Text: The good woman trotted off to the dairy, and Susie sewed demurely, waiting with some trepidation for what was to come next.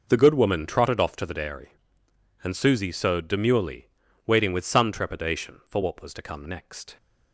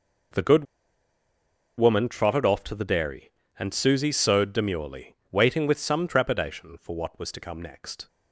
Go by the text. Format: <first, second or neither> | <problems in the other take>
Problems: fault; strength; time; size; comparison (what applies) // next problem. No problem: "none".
first | pauses between "good" and "woman"; at 0.6 s; 1.1 s long